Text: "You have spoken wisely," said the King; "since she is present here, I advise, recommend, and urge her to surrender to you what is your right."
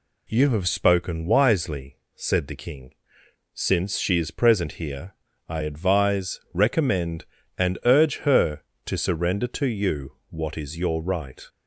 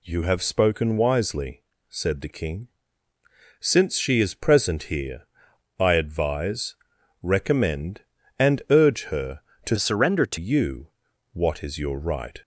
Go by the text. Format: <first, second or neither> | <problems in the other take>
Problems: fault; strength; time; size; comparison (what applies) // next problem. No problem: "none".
first | changes voice from "surrender" to "to"; from 9.7 to 10.3 s; 0.6 s long // pauses between "you" and "what"; at 10.8 s; 0.44 s long